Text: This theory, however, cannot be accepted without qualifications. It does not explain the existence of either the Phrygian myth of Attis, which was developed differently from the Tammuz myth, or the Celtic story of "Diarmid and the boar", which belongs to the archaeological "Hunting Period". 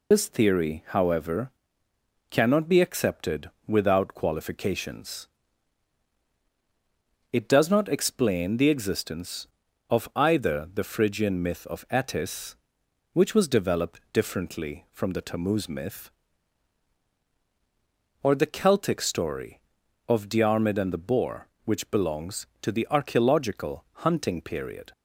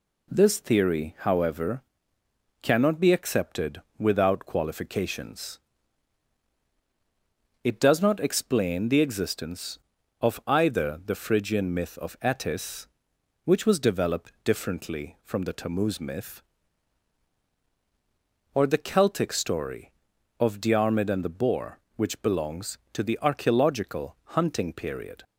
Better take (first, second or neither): second